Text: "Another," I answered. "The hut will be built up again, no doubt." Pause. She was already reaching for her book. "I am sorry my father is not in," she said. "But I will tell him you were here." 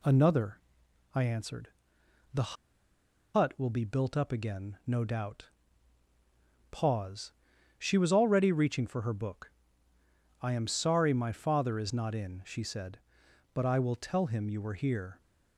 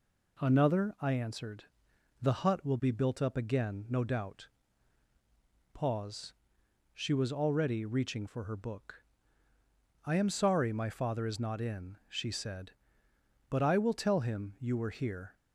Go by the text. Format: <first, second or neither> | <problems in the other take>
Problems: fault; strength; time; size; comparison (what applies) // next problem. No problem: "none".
second | pauses between "The" and "hut"; noticeable; at 2.5 s; 0.80 s long